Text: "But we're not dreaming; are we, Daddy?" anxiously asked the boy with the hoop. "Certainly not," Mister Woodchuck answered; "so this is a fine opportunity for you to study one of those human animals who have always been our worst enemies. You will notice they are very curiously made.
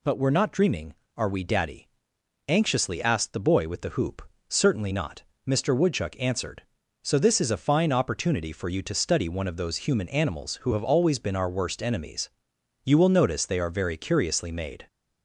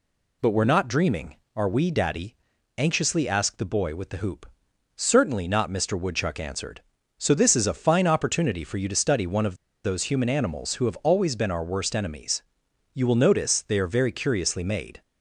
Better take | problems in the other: first | pauses between "of" and "those"; slight; at 9.5 s; 0.29 s long

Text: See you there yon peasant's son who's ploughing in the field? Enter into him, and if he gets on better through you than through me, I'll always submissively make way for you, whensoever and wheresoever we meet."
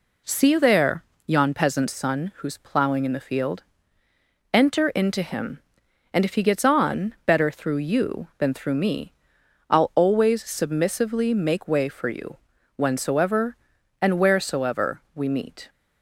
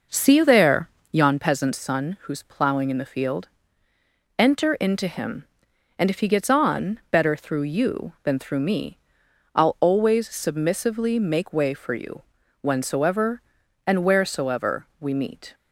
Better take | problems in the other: first | starts louder than the rest; noticeable; until 1.5 s; 5.5 dB // pauses between "there" and "yon"; slight; at 0.8 s; 0.24 s long; slight in the first

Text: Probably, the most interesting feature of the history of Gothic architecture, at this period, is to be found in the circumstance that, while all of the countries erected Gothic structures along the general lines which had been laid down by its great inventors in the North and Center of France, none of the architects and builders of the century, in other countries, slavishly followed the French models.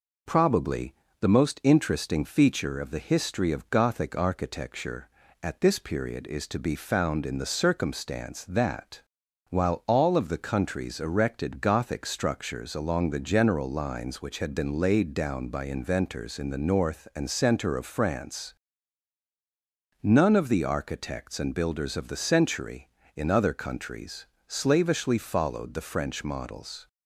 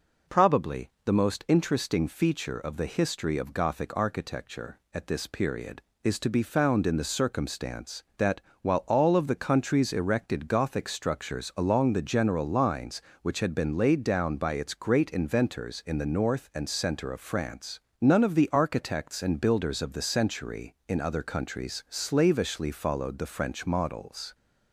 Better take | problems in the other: second | skips "its great"; at 15.6 s

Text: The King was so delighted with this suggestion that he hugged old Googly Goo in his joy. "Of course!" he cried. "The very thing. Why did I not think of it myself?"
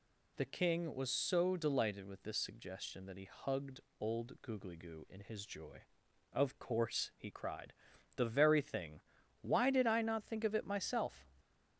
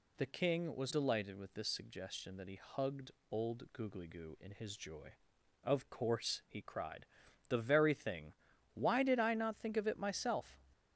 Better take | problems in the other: first | skips "so"; at 0.9 s // pauses between "hugged" and "old"; slight; at 3.1 s; 0.20 s long; slight in the first

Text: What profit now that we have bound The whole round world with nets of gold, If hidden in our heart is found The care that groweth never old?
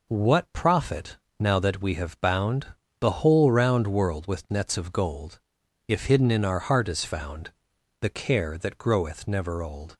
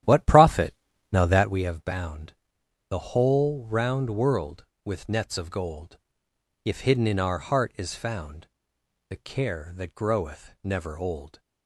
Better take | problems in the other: first | starts louder than the rest; strong; until 1.6 s; 11.5 dB // pauses between "profit" and "now"; at 0.7 s; 0.40 s long; slight in the first // pauses between "bound" and "The"; noticeable; at 2.3 s; 0.56 s long; slight in the first // pauses between "found" and "The"; noticeable; at 8.4 s; 0.62 s long; noticeable in the first

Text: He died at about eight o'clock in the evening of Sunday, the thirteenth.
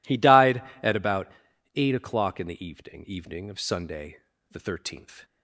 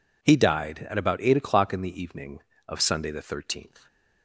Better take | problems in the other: second | pauses between "about" and "eight"; noticeable; at 1.2 s; 0.46 s long // says "evening" twice; at 3.0 s

